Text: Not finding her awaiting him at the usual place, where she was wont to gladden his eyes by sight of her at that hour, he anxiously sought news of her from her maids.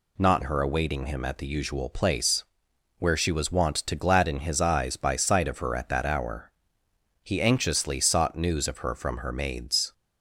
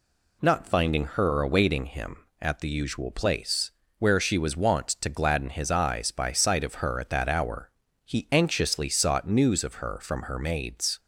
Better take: second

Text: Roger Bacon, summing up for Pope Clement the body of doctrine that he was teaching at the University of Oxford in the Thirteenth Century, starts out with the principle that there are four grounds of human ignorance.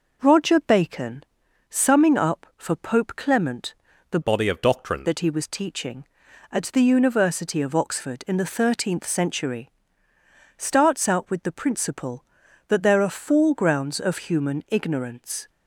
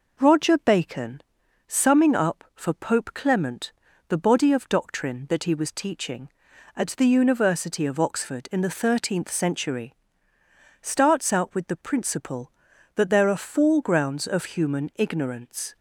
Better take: second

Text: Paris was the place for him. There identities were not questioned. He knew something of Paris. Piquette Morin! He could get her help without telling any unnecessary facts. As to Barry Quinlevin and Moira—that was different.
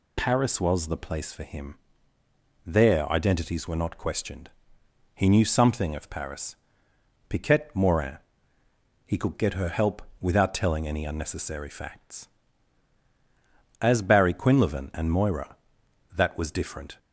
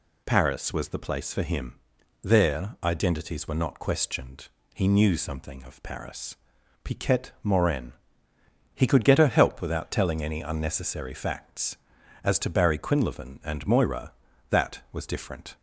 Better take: second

